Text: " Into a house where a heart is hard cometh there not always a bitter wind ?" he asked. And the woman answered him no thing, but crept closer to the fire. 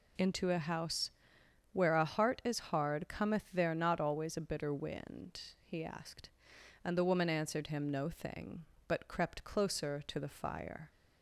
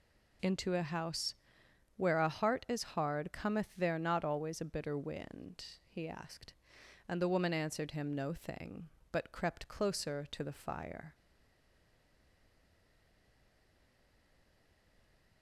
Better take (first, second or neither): first